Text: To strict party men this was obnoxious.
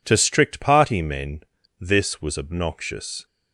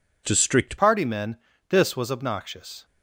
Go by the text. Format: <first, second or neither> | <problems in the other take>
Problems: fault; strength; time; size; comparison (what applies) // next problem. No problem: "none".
first | changes voice at "party"; from 0.7 s on; 2.1 s long // pauses between "men" and "this"; slight; at 1.3 s; 0.32 s long; also in the first